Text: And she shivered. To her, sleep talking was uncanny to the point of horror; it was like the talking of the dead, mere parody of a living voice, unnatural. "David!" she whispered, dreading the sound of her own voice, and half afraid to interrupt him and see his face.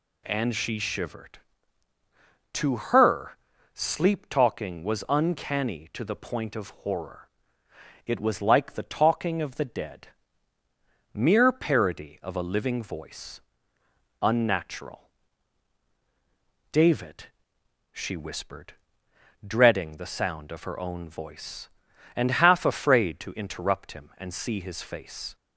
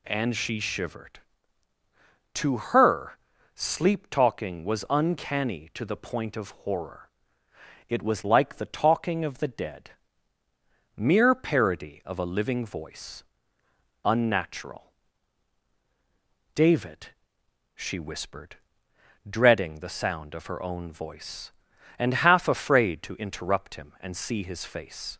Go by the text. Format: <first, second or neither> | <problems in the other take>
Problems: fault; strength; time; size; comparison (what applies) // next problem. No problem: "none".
neither | none